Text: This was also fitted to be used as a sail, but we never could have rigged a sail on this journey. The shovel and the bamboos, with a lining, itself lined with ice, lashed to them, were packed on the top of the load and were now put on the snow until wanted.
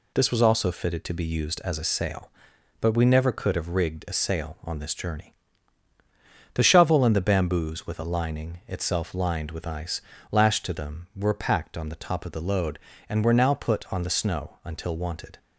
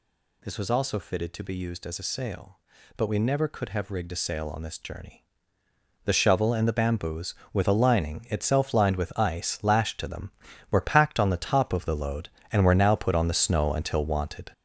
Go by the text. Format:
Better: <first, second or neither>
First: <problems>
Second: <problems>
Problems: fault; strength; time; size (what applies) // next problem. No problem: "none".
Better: first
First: none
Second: gets louder; throughout; 6.5 dB